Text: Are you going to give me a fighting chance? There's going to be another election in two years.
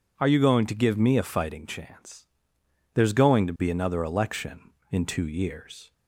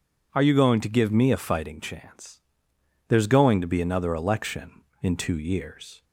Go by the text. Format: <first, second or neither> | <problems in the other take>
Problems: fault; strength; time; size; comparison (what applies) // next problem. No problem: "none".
neither | none